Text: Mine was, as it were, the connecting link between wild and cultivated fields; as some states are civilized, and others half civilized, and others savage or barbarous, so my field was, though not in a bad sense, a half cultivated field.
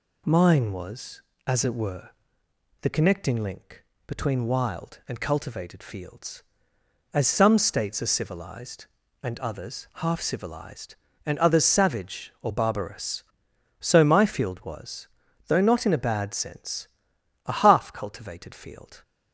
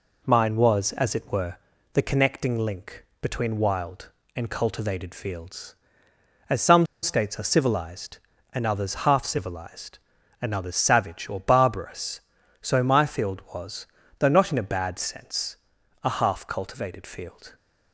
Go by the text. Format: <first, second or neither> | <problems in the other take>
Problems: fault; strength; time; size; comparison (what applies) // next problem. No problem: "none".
first | pauses between "link" and "between"; slight; at 3.0 s; 0.16 s long; slight in the first // pauses between "some" and "states"; slight; at 6.8 s; 0.16 s long